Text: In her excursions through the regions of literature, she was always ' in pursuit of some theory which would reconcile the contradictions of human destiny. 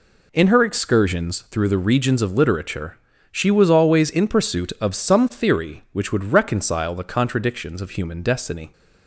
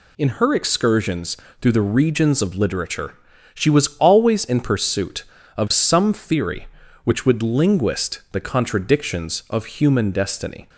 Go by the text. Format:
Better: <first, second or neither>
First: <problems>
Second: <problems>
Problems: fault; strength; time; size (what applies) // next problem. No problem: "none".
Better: first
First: none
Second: pauses between "excursions" and "through"; slight; at 1.3 s; 0.24 s long // says "linguist" for "reconcile"; at 7.4 s